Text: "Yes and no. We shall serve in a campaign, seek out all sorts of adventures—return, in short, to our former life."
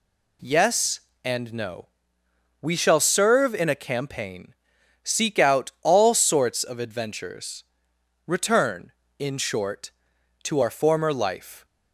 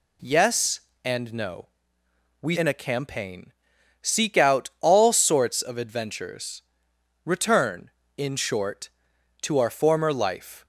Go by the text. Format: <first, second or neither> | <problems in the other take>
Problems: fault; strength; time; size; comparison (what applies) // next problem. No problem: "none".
first | skips "shall serve"; at 2.5 s